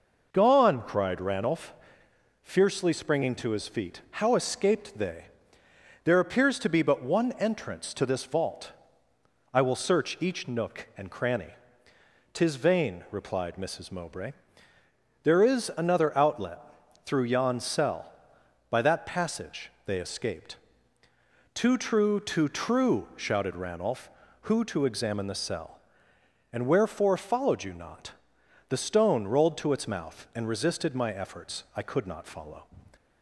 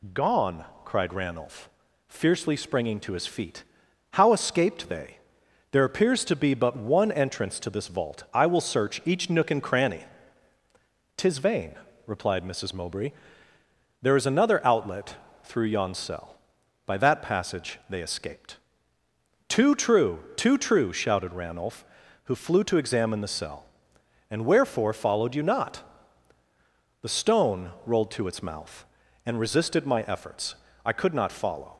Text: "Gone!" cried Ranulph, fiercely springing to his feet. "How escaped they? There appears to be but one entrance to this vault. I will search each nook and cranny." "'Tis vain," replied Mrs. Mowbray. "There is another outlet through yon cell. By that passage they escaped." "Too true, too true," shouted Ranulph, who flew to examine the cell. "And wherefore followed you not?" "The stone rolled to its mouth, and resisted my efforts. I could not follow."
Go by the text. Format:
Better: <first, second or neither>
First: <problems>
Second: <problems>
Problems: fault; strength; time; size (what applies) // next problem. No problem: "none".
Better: second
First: pauses between "outlet" and "through"; at 16.6 s; 0.44 s long // skips "flew"; at 24.6 s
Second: pauses between "outlet" and "through"; slight; at 15.1 s; 0.30 s long